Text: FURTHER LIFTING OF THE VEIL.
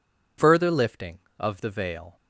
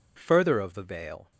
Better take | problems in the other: first | skips "LIFTING"; at 0.5 s

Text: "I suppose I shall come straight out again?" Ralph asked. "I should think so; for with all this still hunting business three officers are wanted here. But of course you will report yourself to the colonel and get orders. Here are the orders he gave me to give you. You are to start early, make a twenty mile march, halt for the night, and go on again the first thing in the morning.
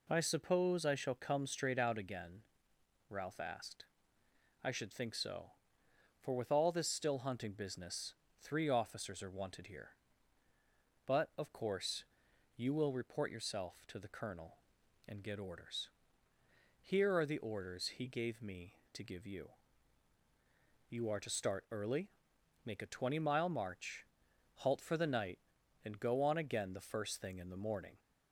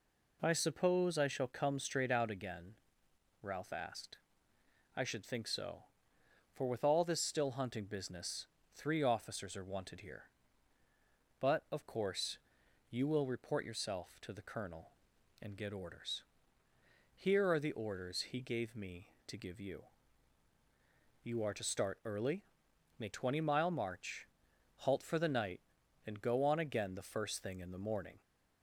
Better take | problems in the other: first | pauses between "business" and "three"; slight; at 8.4 s; 0.28 s long; slight in the first // pauses between "course" and "you"; noticeable; at 12.3 s; 0.50 s long; noticeable in the first // skips "a"; at 23.1 s

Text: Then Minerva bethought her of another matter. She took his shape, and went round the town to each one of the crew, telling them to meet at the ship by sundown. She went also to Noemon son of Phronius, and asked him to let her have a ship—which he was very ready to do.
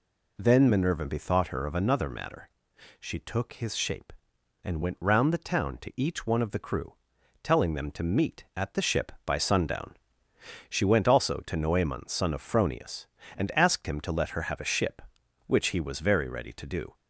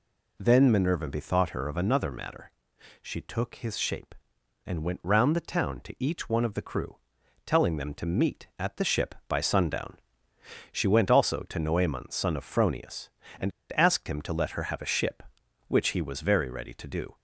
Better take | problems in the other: first | pauses between "and" and "asked"; slight; at 13.5 s; 0.26 s long

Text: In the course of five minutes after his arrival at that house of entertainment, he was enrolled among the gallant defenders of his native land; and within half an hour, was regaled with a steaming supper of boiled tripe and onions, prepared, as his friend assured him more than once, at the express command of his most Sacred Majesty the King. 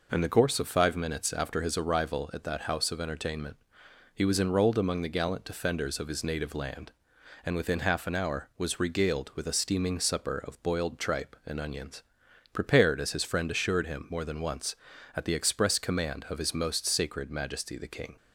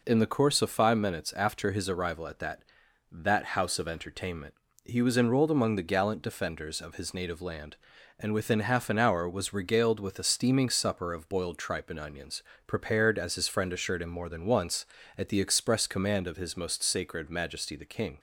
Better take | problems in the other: first | says "that" twice; at 3.1 s

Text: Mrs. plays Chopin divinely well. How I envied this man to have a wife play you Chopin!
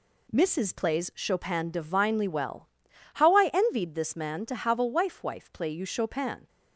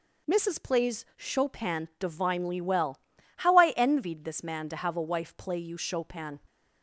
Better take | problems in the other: second | says "wife" twice; at 5.2 s

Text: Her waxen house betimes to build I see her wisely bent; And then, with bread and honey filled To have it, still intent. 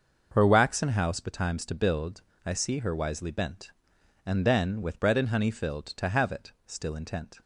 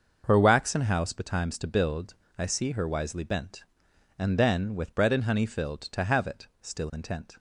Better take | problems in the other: neither | starts louder than the rest; noticeable; the same in both // pauses between "build" and "I"; slight; the same in both

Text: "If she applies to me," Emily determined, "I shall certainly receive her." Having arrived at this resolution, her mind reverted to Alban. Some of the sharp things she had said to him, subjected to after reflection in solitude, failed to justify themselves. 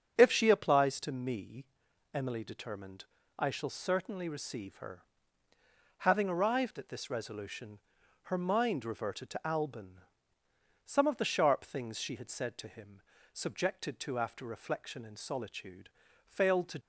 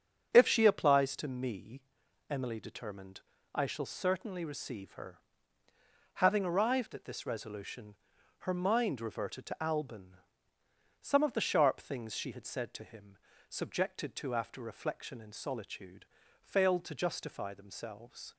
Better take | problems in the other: second | starts louder than the rest; strong; until 1.1 s; 8 dB; strong in the second // stops before "justify themselves"; at 16.8 s

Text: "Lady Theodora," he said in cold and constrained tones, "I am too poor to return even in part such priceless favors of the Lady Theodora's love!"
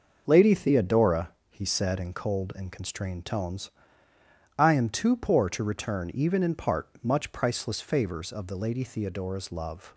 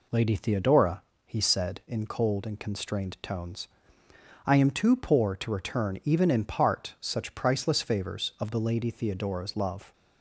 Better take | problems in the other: second | says "much" for "such"; at 7.0 s

